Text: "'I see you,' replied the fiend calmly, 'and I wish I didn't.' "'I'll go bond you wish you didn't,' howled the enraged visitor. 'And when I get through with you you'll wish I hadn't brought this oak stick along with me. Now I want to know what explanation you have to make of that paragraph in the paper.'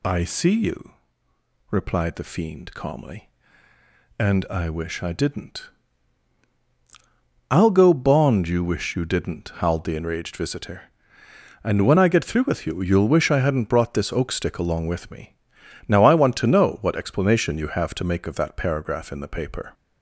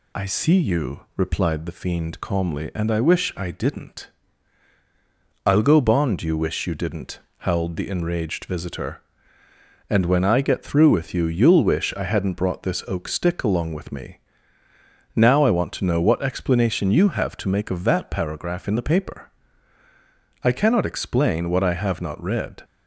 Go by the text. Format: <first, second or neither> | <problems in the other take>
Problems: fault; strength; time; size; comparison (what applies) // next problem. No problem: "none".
first | goes on to say "I cannot explain what I have not read"; strong; from 20.4 s on; 2.2 s long